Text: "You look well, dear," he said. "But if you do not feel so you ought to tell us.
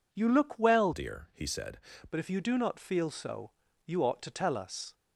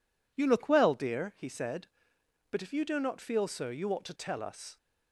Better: second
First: changes voice from "dear" to "said"; from 0.9 to 1.7 s; 0.8 s long // pauses between "so" and "you"; slight; at 3.5 s; 0.34 s long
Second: none

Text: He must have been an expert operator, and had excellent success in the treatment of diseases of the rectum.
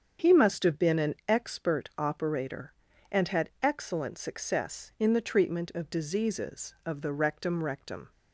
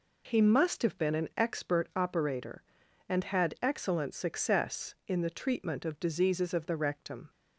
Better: second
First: starts louder than the rest; strong; until 1.3 s; 7.5 dB // says "rectum" twice; at 7.6 s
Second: none

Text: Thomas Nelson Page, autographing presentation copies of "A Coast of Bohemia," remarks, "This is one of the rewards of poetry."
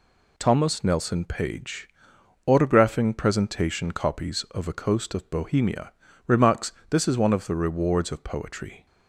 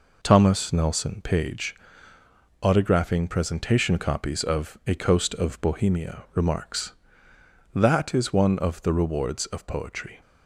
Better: first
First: none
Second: says "That" for "This"; at 7.7 s

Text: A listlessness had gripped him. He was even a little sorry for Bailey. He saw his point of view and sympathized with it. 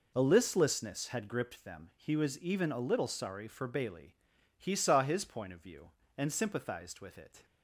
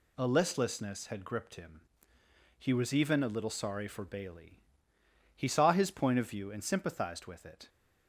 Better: second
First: says "them" for "him"; at 1.6 s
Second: none

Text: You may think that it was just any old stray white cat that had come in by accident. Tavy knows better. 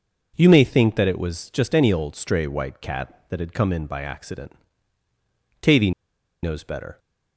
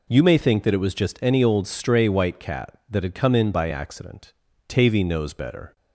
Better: second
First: pauses between "Tavy" and "knows"; noticeable; at 5.9 s; 0.52 s long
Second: none

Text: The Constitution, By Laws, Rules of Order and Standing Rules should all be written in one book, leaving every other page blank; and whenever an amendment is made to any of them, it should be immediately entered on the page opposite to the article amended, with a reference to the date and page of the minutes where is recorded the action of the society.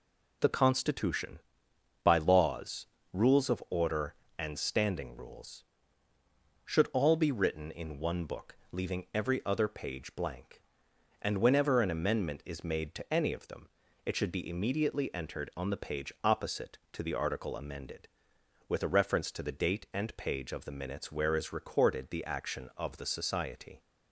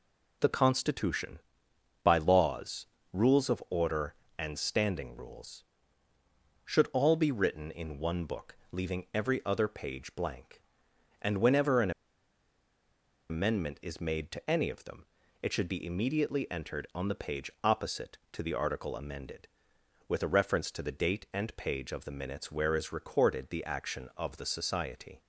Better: first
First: none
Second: pauses between "an" and "amendment"; strong; at 11.9 s; 1.3 s long

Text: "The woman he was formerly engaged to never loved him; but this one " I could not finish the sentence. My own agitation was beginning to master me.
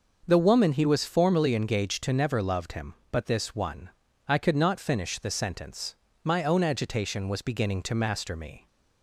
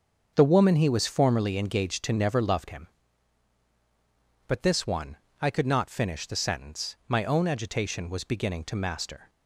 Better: first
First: starts louder than the rest; until 1.2 s; 6.5 dB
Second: starts louder than the rest; until 1.3 s; 7 dB // stops before "me"; at 9.2 s

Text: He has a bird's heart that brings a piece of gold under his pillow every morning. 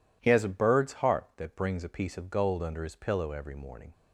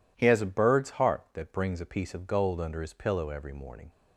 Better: neither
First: none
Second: none

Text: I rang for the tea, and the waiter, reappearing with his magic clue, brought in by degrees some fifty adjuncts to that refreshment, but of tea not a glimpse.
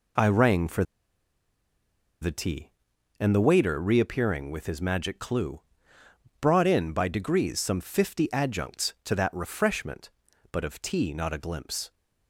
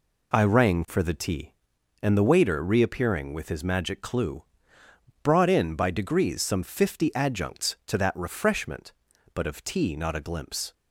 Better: second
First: pauses between "for" and "the"; strong; at 0.8 s; 1.3 s long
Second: none

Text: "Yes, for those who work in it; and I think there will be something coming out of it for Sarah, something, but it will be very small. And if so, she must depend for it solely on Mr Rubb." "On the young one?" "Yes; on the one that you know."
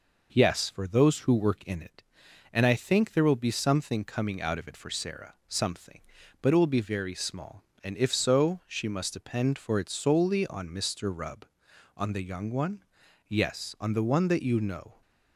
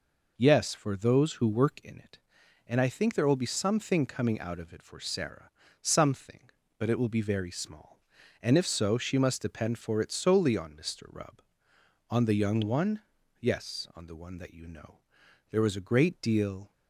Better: first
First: none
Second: goes on to say "There was a great deal"; noticeable; from 15.5 s on; 1.2 s long

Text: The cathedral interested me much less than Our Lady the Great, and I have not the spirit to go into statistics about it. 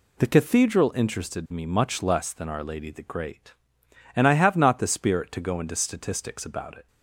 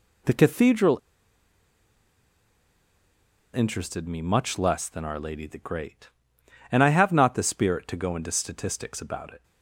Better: first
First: none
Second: pauses between "cathedral" and "interested"; strong; at 0.9 s; 2.5 s long

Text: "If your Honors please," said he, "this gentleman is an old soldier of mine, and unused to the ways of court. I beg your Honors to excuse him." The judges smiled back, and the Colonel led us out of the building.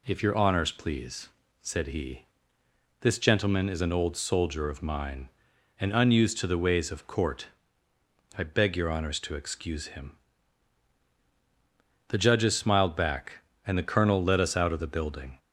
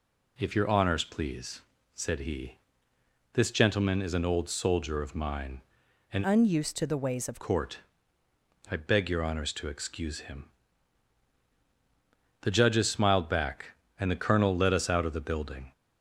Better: first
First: none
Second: changes voice from "unused" to "of"; from 6.2 to 7.4 s; 1.2 s long

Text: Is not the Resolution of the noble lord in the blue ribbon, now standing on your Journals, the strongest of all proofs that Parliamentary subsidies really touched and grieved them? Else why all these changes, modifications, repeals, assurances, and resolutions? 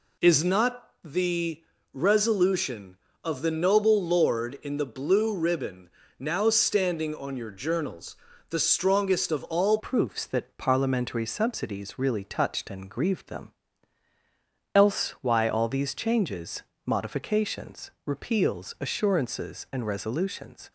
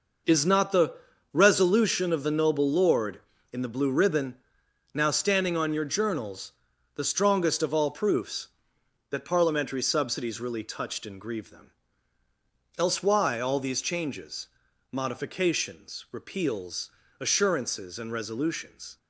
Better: second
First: pauses between "the" and "Resolution"; slight; at 1.6 s; 0.32 s long // changes voice at "proofs"; from 9.7 s on; 11.0 s long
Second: pauses between "the" and "Resolution"; at 0.9 s; 0.40 s long

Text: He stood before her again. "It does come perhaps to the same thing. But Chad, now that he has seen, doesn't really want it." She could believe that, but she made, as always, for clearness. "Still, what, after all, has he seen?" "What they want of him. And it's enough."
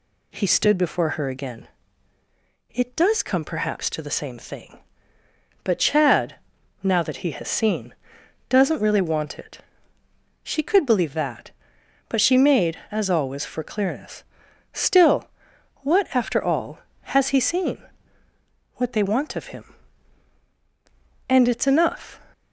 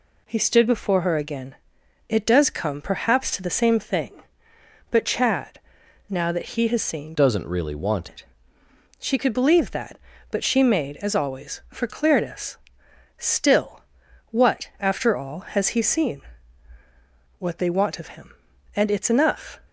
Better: first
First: none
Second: changes voice from "doesn't" to "want"; from 7.1 to 8.0 s; 0.9 s long

